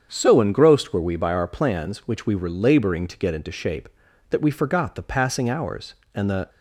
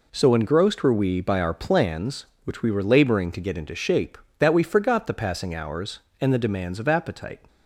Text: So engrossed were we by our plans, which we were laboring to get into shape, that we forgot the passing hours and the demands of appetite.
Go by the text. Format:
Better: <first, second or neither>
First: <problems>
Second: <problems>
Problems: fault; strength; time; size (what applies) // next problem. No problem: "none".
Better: second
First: starts louder than the rest; strong; until 1.1 s; 7.5 dB // stops before "demands of appetite"; at 6.4 s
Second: none